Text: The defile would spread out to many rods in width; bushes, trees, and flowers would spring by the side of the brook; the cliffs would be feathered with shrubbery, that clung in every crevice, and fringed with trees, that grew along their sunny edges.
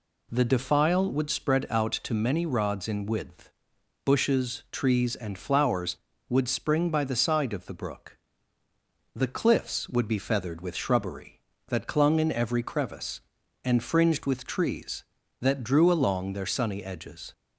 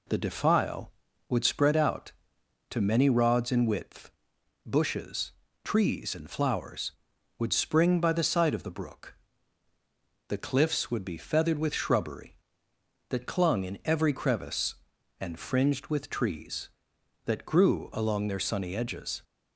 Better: second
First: says "drew" for "grew"; at 15.6 s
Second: none

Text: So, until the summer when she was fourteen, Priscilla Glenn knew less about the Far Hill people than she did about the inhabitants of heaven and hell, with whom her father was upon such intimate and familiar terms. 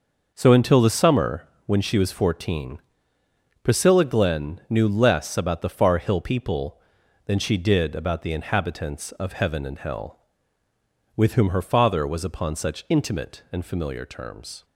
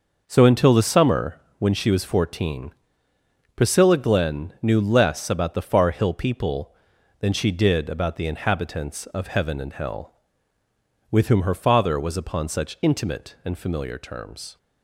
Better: neither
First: starts louder than the rest; noticeable; until 1.3 s; 6 dB // pauses between "summer" and "when"; slight; at 1.4 s; 0.20 s long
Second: starts louder than the rest; noticeable; until 1.2 s; 6 dB // pauses between "summer" and "when"; slight; at 1.3 s; 0.20 s long

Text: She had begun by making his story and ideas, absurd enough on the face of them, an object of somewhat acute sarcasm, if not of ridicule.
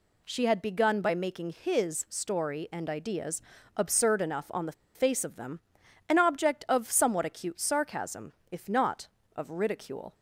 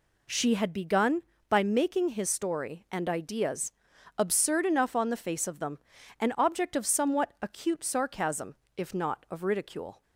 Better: second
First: pauses between "the" and "face"; slight; at 4.7 s; 0.23 s long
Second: none

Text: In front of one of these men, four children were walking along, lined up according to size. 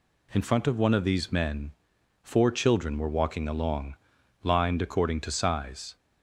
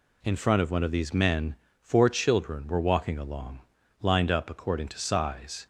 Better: second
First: skips "up"; at 4.7 s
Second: none

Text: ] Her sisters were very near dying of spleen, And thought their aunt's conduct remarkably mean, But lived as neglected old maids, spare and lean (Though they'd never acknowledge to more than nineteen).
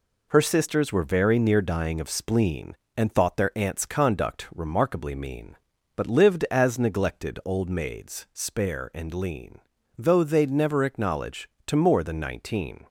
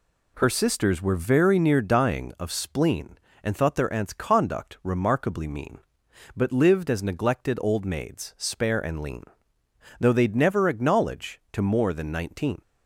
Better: neither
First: none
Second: none

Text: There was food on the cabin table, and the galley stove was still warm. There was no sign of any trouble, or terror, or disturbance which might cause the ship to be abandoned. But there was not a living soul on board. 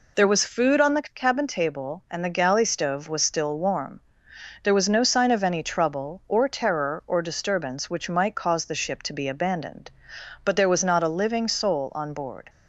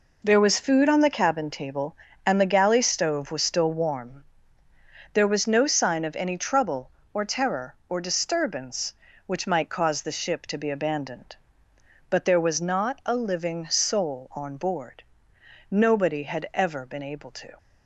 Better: first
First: none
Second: goes on to say "Nobody had ever been able to"; strong; from 15.6 s on; 1.8 s long

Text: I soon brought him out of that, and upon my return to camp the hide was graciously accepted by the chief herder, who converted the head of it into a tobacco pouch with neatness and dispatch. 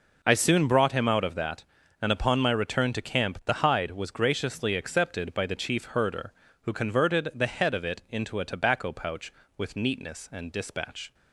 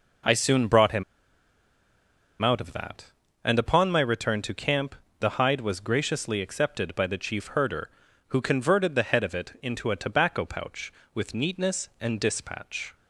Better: first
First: none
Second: pauses between "him" and "out"; strong; at 1.0 s; 1.3 s long // pauses between "camp" and "the"; slight; at 4.9 s; 0.24 s long

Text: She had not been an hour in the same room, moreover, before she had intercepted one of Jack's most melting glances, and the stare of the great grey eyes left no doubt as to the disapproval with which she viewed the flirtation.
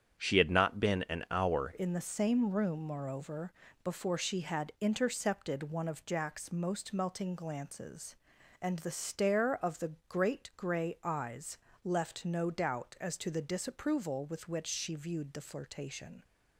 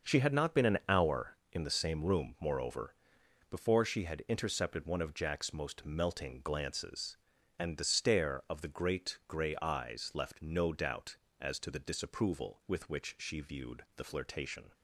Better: second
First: starts louder than the rest; strong; until 1.1 s; 8.5 dB // changes voice at "in"; from 1.7 s on; 14.5 s long // pauses between "the" and "great"; slight; at 9.9 s; 0.16 s long // pauses between "eyes" and "left"; slight; at 11.5 s; 0.28 s long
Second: starts louder than the rest; until 1.0 s; 6 dB

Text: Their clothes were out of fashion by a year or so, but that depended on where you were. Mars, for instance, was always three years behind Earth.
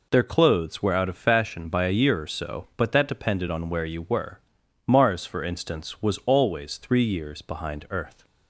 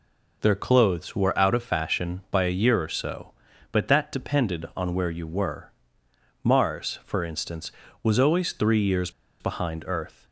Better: first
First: none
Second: pauses between "years" and "behind"; slight; at 9.0 s; 0.30 s long

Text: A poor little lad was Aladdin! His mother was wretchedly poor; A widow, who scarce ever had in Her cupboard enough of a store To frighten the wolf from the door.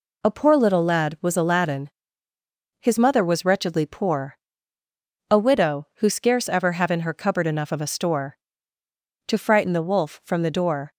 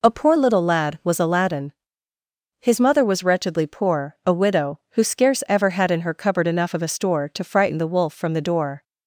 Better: second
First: says "have" for "had"; at 6.7 s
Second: none

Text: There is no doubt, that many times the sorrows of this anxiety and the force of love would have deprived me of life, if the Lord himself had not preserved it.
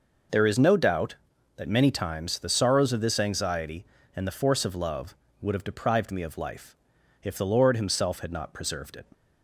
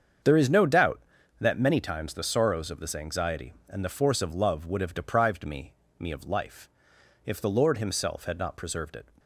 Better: first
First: none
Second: starts louder than the rest; strong; until 1.6 s; 7 dB // says "me" twice; at 5.9 s

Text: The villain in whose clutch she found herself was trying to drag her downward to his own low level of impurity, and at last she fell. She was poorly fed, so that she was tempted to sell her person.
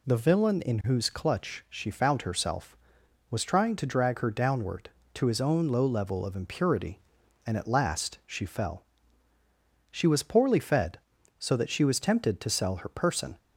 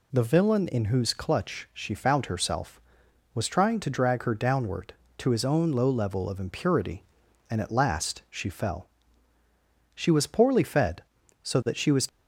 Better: first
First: none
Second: stops before "tempted to sell her person"; at 12.0 s

